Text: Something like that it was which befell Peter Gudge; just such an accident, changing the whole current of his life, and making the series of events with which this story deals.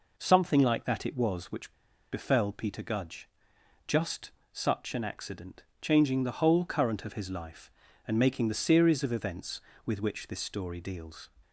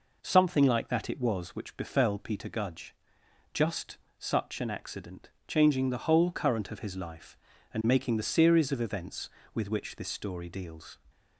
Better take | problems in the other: second | pauses between "which" and "befell"; at 1.7 s; 0.39 s long // pauses between "just" and "such"; slight; at 4.3 s; 0.20 s long; slight in the second

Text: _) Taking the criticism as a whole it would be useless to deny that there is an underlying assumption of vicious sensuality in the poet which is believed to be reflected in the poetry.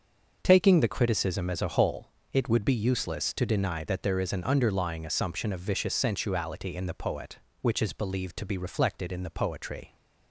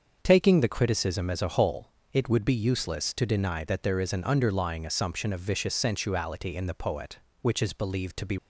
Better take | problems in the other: first | starts louder than the rest; until 1.2 s; 6.5 dB; also in the first // pauses between "whole" and "it"; slight; at 1.9 s; 0.20 s long; slight in the first // stops before "reflected in the poetry"; at 8.3 s

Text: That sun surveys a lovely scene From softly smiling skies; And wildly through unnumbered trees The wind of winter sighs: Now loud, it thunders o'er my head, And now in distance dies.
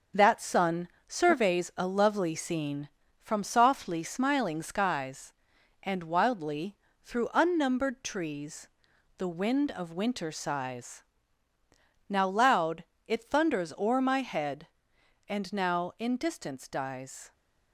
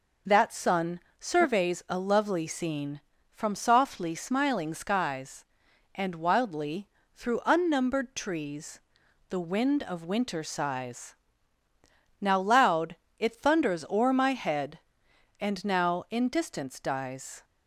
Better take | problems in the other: second | gets quieter; noticeable; throughout; 5 dB // pauses between "sun" and "surveys"; slight; at 0.8 s; 0.22 s long; slight in the second // pauses between "wildly" and "through"; slight; at 6.7 s; 0.26 s long; slight in the second // pauses between "trees" and "The"; noticeable; at 8.6 s; 0.48 s long; noticeable in the second

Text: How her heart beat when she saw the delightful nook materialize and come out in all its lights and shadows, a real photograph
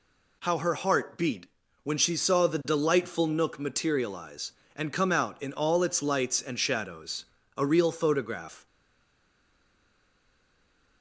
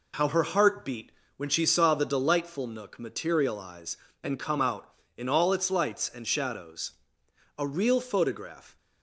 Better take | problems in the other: second | pauses between "beat" and "when"; slight; at 1.4 s; 0.36 s long; slight in the second // stays silent after the last word; from 8.6 s on; 2.4 s long

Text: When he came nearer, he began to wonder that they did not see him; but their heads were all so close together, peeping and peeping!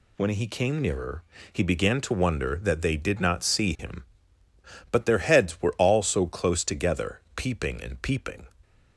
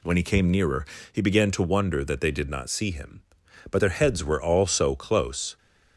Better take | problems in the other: first | stops before "together peeping and peeping"; at 5.5 s

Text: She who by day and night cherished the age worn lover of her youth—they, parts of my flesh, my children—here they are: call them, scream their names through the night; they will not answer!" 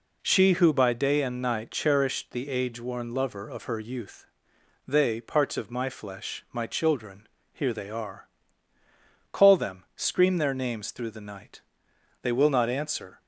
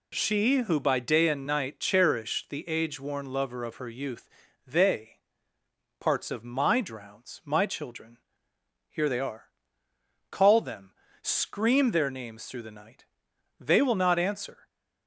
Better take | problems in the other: first | says "drowns" for "flesh"; at 6.8 s

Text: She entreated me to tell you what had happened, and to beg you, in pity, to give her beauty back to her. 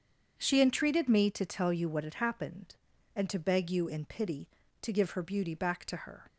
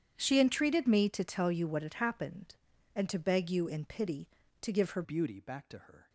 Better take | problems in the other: first | starts louder than the rest; strong; until 1.1 s; 9 dB; strong in the first // changes voice at "beauty"; from 5.0 s on; 1.0 s long

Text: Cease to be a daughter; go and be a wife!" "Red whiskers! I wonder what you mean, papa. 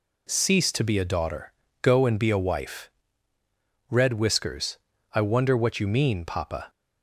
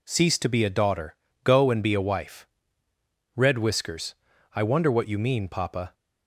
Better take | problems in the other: neither | none

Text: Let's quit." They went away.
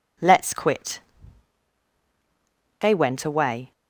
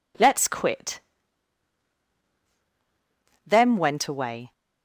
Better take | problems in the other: first | says "Them" for "They"; at 3.4 s

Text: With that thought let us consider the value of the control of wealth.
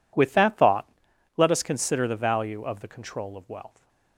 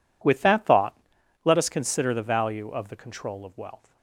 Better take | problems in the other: neither | pauses between "thought" and "let"; noticeable; the same in both

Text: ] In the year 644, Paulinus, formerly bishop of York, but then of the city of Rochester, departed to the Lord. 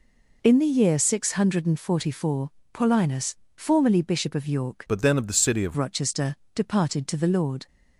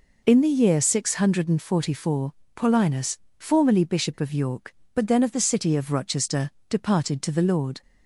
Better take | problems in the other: second | changes voice from "but" to "of"; from 4.8 to 5.7 s; 0.9 s long

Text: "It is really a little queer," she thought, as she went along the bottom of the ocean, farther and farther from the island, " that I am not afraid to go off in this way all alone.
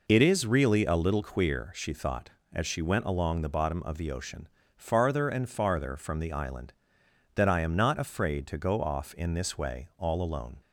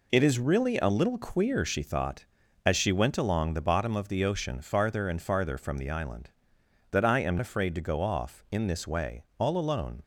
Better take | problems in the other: first | skips "not"; at 7.3 s // pauses between "way" and "all"; slight; at 9.2 s; 0.16 s long

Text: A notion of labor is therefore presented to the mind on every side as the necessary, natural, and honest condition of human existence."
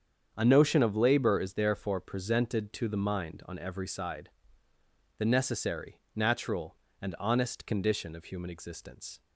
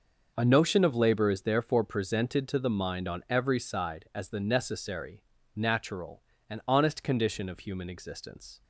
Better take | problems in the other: second | starts louder than the rest; strong; until 1.3 s; 7.5 dB; noticeable in the second // skips "as"; at 4.7 s

